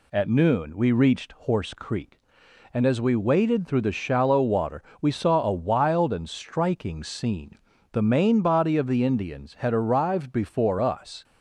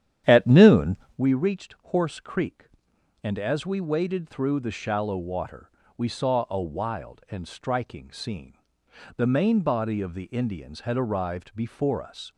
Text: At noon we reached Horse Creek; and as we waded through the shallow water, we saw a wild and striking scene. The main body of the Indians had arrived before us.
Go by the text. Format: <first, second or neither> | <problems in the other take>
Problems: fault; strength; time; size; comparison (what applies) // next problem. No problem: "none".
first | starts louder than the rest; strong; until 1.2 s; 10 dB // pauses between "noon" and "we"; slight; at 0.9 s; 0.22 s long